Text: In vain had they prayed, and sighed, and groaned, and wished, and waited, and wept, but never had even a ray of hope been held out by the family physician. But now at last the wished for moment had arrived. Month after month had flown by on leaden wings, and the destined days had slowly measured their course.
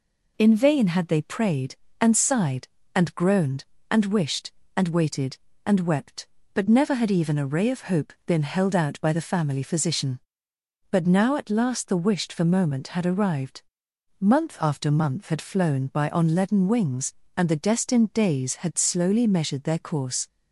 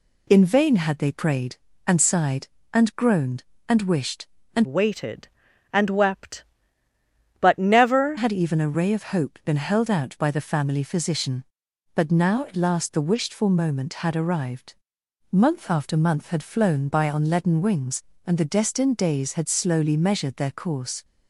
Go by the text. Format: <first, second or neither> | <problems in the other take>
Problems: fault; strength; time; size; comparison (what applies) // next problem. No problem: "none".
first | changes voice from "waited" to "never"; from 4.6 to 8.1 s; 3.5 s long